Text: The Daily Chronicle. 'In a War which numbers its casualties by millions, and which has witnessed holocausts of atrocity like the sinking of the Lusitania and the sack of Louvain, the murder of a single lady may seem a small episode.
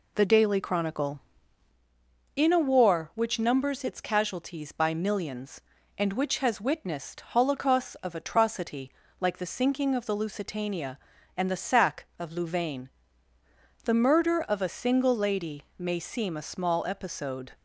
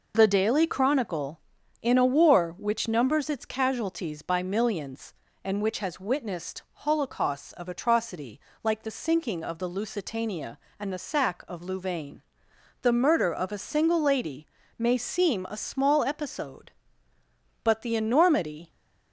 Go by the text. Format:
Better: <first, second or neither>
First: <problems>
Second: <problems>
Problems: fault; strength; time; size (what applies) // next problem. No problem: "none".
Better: first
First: pauses between "atrocity" and "like"; slight; at 8.9 s; 0.28 s long // pauses between "lady" and "may"; slight; at 15.6 s; 0.16 s long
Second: pauses between "atrocity" and "like"; slight; at 8.3 s; 0.24 s long // pauses between "lady" and "may"; slight; at 14.4 s; 0.32 s long // goes on to say "But the enormity"; noticeable; from 17.6 s on; 1.0 s long